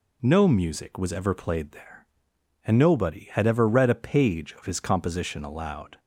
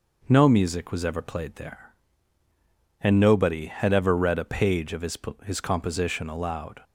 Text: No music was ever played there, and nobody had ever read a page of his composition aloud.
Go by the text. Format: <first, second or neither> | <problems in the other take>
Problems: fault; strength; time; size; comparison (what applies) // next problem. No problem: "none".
first | says "his" twice; at 5.4 s